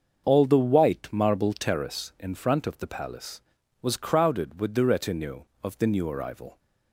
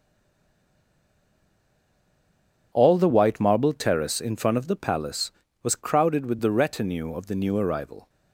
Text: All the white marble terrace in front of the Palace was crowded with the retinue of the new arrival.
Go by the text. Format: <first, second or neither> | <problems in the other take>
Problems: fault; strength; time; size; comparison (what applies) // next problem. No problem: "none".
first | stays silent before the first word; strong; until 2.7 s; 2.7 s long // starts louder than the rest; strong; until 3.7 s; 8.5 dB; also in the first